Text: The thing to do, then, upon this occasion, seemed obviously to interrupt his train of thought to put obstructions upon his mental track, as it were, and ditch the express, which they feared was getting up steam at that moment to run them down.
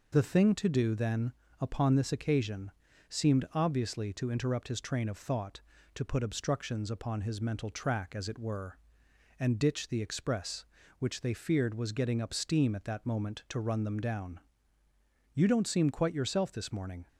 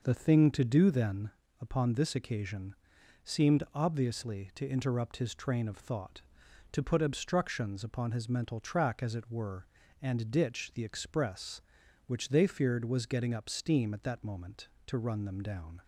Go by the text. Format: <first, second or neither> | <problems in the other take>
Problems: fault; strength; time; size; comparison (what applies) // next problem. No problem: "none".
second | goes on to say "You don't seem quite yourself this morning"; strong; from 15.3 s on; 1.7 s long